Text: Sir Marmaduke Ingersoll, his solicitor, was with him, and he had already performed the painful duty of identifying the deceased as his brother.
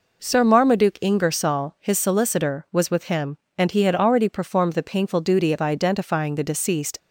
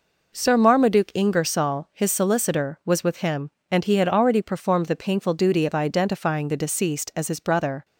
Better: second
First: stops before "as his brother"; at 6.9 s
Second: none

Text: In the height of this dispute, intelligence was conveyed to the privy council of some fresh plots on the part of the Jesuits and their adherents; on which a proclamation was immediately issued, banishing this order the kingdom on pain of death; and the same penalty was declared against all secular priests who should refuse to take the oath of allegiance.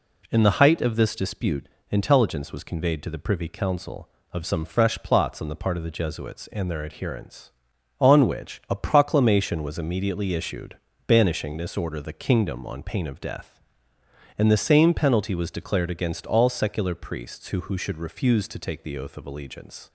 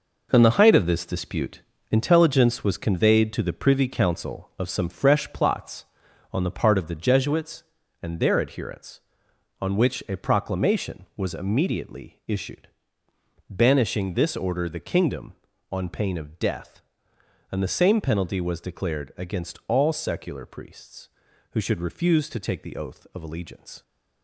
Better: second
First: says "who" twice; at 17.6 s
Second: none

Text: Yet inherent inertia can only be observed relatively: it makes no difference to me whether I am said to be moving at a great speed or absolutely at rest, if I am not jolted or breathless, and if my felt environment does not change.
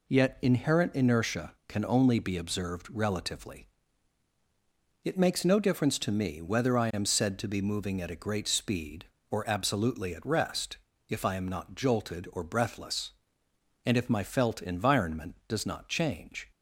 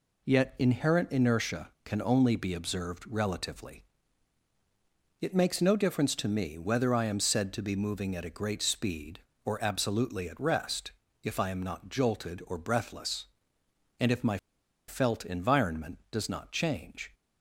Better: first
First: none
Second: pauses between "my" and "felt"; noticeable; at 14.3 s; 0.51 s long

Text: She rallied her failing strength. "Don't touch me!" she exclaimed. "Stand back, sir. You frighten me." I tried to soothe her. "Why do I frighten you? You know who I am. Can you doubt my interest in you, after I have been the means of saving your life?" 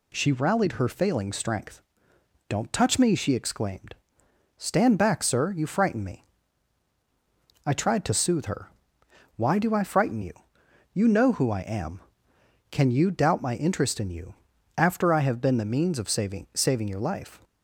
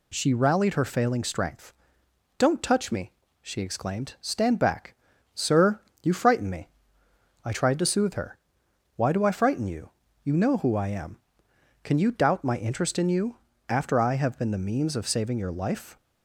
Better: second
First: says "saving" twice; at 16.5 s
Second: none

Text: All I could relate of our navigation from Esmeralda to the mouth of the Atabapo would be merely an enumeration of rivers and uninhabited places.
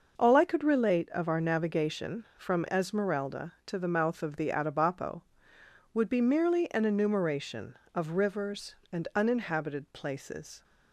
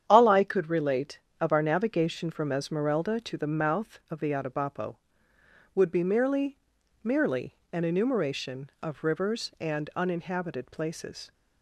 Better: first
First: none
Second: starts louder than the rest; strong; until 1.0 s; 9 dB // says "merely" twice; at 7.0 s

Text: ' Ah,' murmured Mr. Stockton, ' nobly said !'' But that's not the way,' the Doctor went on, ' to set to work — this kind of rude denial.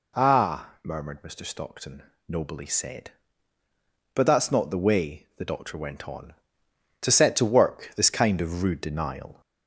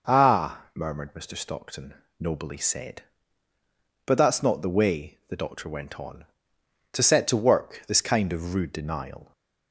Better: second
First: gets louder; slight; throughout; 2.5 dB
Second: none

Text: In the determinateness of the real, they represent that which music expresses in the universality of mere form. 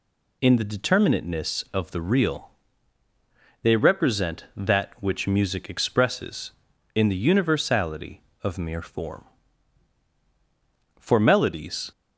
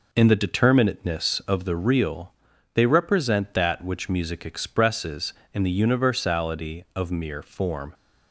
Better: second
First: goes on to say "For melodies"; noticeable; from 10.9 s on; 0.94 s long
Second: none

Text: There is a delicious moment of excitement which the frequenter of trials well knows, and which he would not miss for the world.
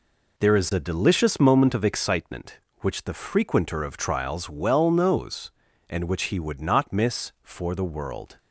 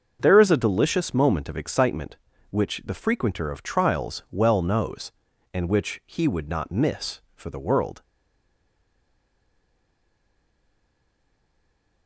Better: first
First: none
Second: starts louder than the rest; until 1.2 s; 6.5 dB // stays silent after the last word; strong; from 8.0 s on; 4.0 s long

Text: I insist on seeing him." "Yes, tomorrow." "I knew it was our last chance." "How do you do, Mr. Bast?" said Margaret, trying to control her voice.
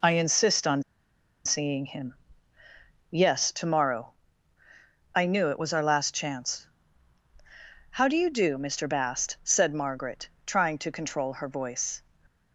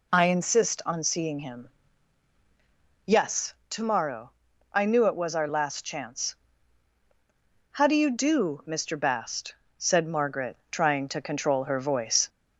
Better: second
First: pauses between "on" and "seeing"; noticeable; at 0.8 s; 0.62 s long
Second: none

